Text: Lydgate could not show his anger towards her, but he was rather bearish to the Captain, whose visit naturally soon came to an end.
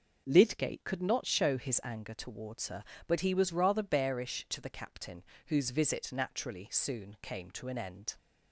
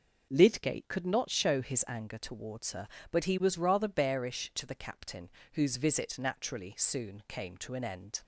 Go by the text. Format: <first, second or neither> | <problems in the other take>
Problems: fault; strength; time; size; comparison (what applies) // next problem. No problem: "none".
neither | none